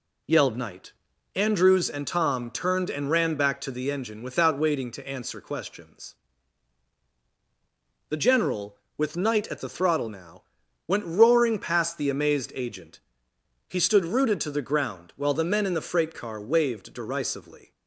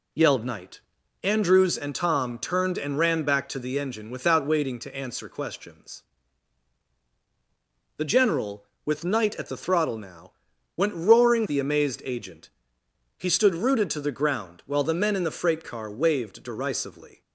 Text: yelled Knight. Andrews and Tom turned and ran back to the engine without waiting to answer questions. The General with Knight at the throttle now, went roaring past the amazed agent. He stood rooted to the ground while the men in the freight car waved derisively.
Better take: first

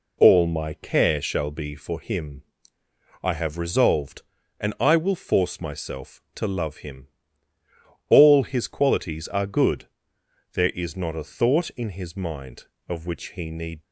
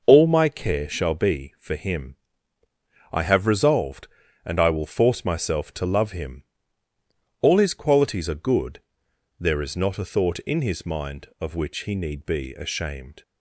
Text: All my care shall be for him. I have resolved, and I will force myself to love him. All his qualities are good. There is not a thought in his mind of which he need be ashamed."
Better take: second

